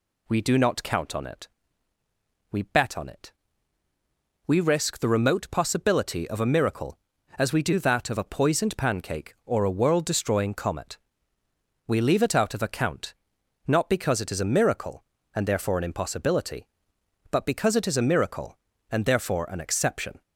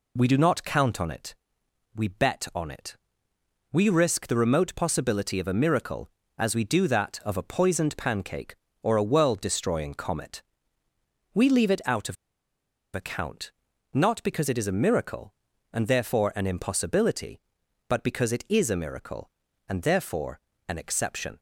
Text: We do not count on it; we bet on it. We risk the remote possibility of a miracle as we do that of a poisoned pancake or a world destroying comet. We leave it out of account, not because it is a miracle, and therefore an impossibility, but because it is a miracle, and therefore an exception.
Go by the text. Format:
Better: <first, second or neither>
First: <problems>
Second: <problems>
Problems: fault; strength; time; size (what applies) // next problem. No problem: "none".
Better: first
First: none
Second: pauses between "of" and "account"; noticeable; at 12.1 s; 0.79 s long // pauses between "therefore" and "an"; slight; at 20.3 s; 0.30 s long